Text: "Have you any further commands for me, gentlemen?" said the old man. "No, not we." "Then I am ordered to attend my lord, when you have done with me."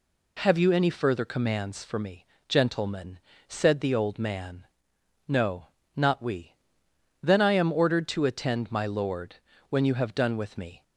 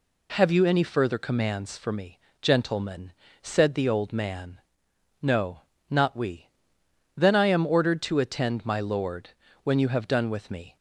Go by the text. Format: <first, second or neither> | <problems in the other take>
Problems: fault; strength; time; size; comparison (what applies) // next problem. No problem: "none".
neither | none